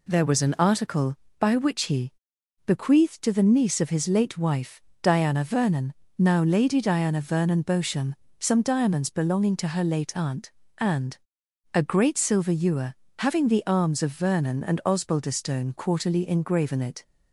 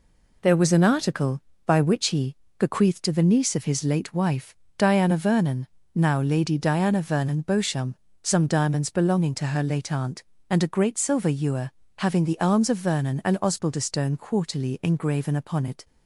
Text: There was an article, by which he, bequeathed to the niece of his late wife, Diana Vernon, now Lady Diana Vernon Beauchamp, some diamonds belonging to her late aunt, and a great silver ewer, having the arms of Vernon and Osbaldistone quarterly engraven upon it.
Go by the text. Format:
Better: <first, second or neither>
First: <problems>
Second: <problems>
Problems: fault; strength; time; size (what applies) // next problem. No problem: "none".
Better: second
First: pauses between "and" and "a"; noticeable; at 11.1 s; 0.56 s long // skips "upon"; at 16.7 s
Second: none